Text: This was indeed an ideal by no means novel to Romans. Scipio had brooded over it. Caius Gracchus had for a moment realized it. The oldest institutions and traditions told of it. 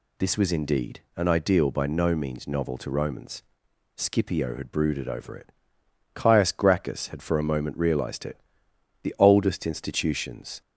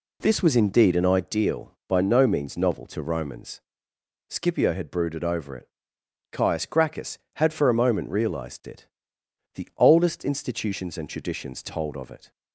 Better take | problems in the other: second | pauses between "indeed" and "an"; slight; at 1.0 s; 0.15 s long // stops before "and traditions told of it"; at 10.6 s

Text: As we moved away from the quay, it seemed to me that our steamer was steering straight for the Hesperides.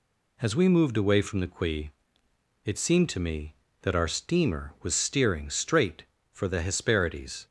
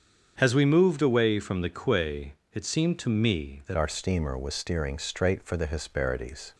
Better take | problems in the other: first | starts louder than the rest; strong; until 1.3 s; 7.5 dB // changes voice at "our"; from 3.7 s on; 2.8 s long

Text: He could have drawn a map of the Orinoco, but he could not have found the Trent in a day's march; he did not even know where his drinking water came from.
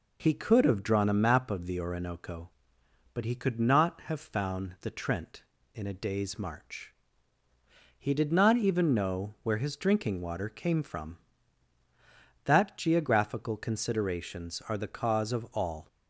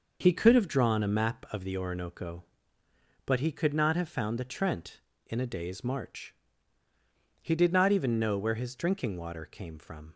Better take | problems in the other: second | goes on to say "That geographical considerations are the cause of all"; strong; from 12.4 s on; 3.4 s long

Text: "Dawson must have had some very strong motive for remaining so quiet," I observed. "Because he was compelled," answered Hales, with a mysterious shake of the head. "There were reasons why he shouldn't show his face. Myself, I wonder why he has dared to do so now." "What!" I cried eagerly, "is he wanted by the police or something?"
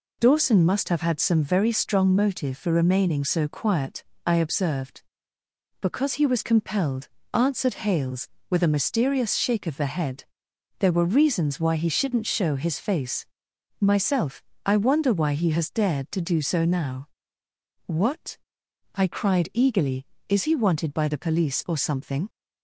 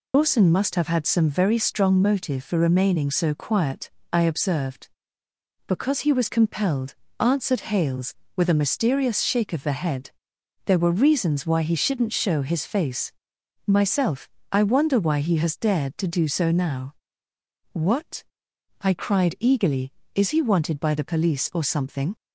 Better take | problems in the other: first | loses the start of "Dawson"; at 0.1 s; 75 ms

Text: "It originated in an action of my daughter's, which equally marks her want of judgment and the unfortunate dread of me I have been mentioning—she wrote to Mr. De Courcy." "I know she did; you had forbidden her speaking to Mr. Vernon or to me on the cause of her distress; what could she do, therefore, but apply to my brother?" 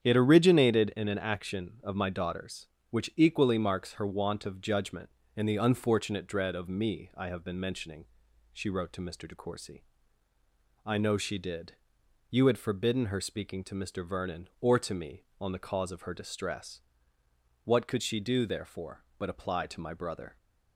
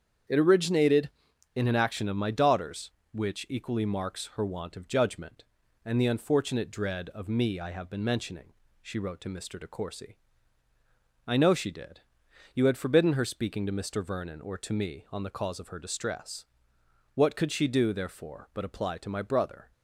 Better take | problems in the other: neither | starts louder than the rest; strong; the same in both

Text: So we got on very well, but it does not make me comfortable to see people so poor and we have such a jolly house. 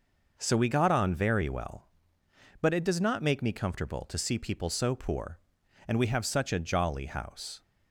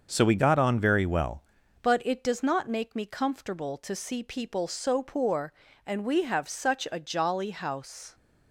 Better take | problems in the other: first | starts louder than the rest; until 1.1 s; 6.5 dB // changes voice at "but"; from 1.8 s on; 6.3 s long

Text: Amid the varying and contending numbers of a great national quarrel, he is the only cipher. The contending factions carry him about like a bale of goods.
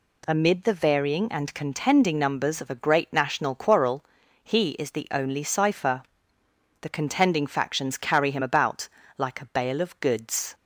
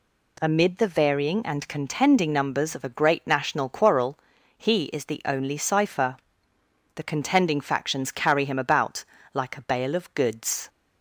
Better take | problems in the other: neither | pauses between "about" and "like"; slight; the same in both

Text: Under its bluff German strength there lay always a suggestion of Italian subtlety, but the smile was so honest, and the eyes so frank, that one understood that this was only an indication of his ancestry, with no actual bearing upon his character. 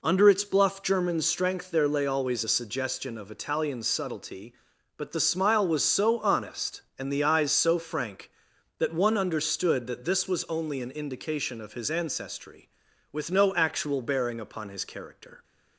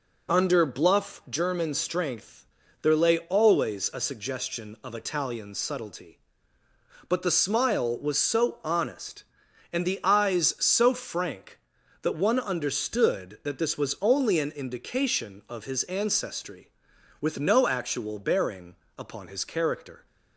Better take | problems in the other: first | skips "its"; at 0.6 s // pauses between "strength" and "there"; at 2.4 s; 0.38 s long // pauses between "bearing" and "upon"; slight; at 18.7 s; 0.22 s long

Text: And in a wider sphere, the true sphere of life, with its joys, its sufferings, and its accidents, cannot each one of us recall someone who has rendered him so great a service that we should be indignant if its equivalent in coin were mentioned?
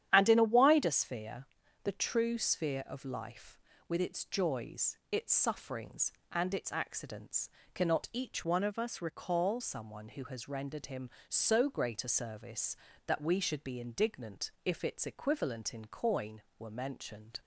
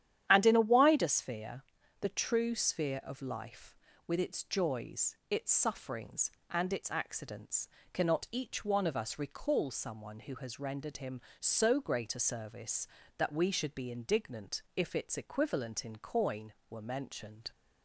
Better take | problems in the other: second | starts louder than the rest; strong; until 1.1 s; 10 dB; strong in the second // changes voice from "one" to "recall"; from 8.4 to 9.6 s; 1.2 s long // pauses between "indignant" and "if"; slight; at 14.4 s; 0.16 s long; slight in the second

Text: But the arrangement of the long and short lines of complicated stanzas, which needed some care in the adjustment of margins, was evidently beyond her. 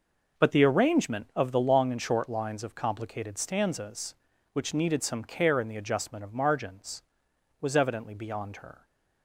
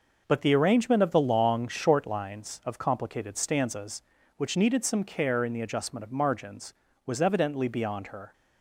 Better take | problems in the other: first | skips "and"; at 1.6 s

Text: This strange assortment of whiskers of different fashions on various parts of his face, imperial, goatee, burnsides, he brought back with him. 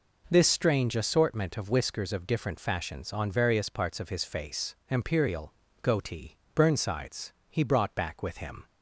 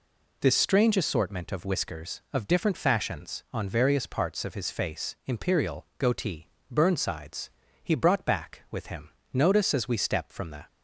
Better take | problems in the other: first | goes on to say "Notice as we step from the"; from 9.3 s on; 1.3 s long

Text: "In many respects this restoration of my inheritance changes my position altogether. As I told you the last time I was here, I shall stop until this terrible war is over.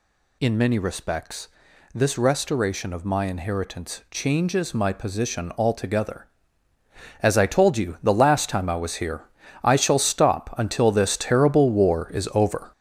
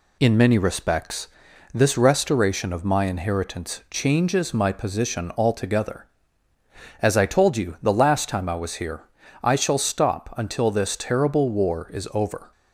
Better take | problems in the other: second | gets louder; throughout; 6.5 dB // pauses between "respects" and "this"; noticeable; at 1.4 s; 0.46 s long; noticeable in the second

